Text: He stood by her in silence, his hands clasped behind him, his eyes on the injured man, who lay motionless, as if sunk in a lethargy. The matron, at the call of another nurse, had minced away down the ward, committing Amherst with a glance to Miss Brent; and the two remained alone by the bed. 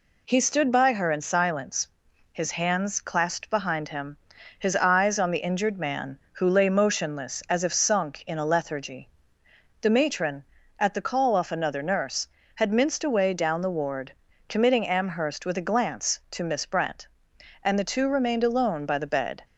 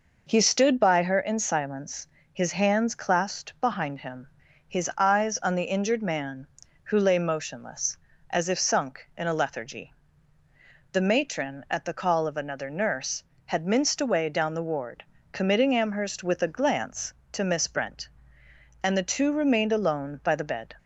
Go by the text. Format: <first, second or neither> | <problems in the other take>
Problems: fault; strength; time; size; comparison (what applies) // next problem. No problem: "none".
second | says "off" for "of"; at 11.3 s